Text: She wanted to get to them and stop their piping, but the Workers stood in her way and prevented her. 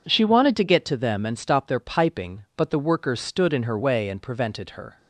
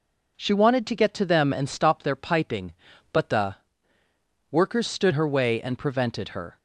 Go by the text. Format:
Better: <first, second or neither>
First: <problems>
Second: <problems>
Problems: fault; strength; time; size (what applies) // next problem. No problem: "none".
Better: first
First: none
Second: pauses between "the" and "Workers"; noticeable; at 3.5 s; 0.96 s long // skips "in"; at 5.1 s